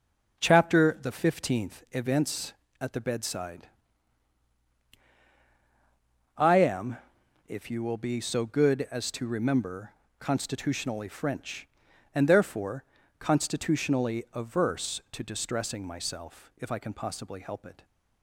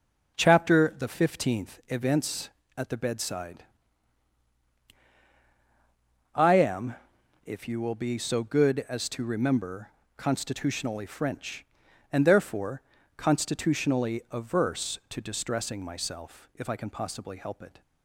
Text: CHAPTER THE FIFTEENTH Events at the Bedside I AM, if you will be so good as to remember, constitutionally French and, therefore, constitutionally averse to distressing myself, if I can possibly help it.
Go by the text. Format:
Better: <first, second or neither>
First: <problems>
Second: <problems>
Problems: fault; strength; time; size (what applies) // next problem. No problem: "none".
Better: neither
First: pauses between "Bedside" and "I"; strong; at 3.6 s; 2.7 s long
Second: pauses between "Bedside" and "I"; strong; at 3.6 s; 2.7 s long